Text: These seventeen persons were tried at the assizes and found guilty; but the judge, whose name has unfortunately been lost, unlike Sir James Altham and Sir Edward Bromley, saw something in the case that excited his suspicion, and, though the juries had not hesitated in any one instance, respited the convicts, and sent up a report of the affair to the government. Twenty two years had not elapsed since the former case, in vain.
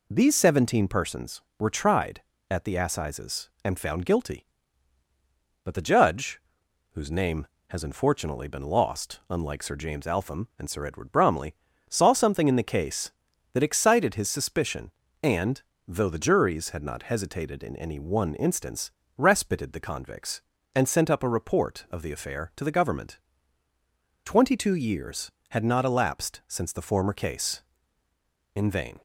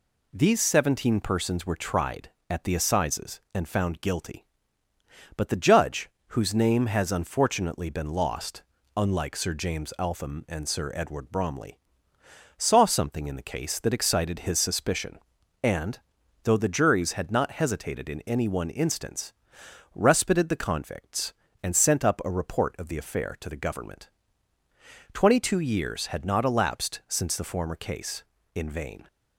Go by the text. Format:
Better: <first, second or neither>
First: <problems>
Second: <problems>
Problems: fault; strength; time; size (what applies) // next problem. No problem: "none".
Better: neither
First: none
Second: none